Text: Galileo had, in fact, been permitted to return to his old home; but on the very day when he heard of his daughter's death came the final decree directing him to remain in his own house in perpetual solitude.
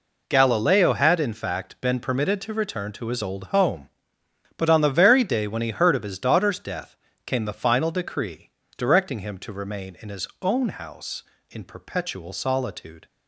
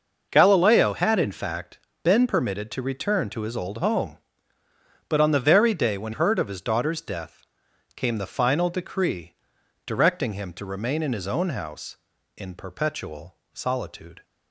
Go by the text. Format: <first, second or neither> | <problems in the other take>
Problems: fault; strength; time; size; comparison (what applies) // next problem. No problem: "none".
first | skips "he"; at 6.1 s // pauses between "death" and "came"; noticeable; at 7.4 s; 0.54 s long; slight in the first // pauses between "decree" and "directing"; noticeable; at 9.3 s; 0.52 s long; slight in the first // pauses between "perpetual" and "solitude"; slight; at 13.3 s; 0.16 s long